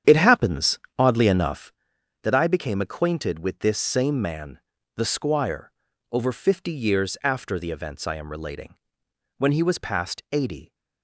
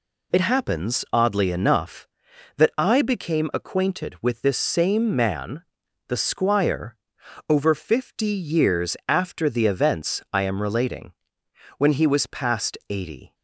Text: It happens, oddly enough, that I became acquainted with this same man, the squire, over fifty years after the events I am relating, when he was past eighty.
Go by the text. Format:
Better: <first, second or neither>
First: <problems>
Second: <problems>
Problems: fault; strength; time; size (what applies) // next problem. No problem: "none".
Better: second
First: starts louder than the rest; strong; until 1.8 s; 9 dB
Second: none